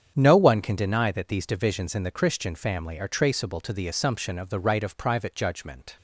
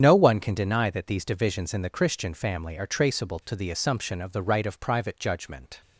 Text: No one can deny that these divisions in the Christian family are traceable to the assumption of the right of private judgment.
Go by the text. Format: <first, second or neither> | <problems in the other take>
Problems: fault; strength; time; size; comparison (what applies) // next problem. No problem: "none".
first | loses the start of "No"; at 0.0 s; 60 ms // starts louder than the rest; strong; until 1.0 s; 8 dB; strong in the first